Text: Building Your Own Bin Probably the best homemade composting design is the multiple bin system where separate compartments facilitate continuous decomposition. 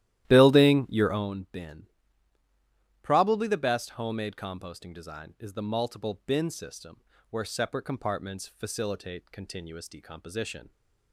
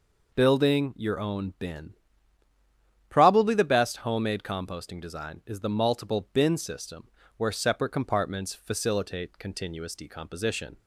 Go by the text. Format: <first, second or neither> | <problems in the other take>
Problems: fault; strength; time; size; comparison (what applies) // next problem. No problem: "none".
second | starts louder than the rest; strong; until 1.4 s; 13.5 dB // pauses between "Bin" and "Probably"; at 1.8 s; 1.2 s long; also in the second // pauses between "system" and "where"; slight; at 6.9 s; 0.32 s long; slight in the second